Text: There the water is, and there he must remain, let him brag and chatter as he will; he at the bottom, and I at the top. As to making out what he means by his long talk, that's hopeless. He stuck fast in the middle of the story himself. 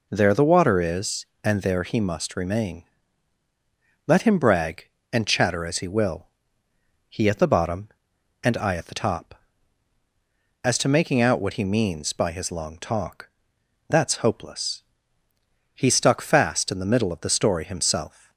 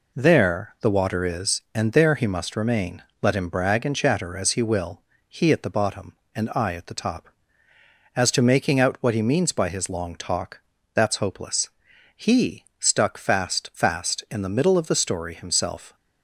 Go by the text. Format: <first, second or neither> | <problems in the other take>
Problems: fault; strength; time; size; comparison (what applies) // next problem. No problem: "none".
first | pauses between "He" and "stuck"; slight; at 12.6 s; 0.16 s long // says "fast" twice; at 13.7 s